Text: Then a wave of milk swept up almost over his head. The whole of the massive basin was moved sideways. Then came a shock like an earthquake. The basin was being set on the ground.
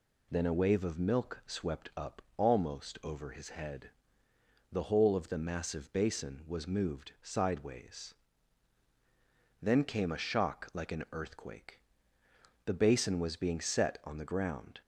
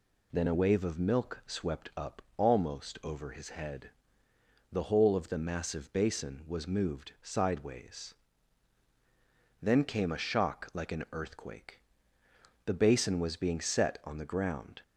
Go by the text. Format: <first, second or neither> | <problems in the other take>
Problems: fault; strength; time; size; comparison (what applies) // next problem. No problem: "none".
neither | pauses between "up" and "almost"; slight; the same in both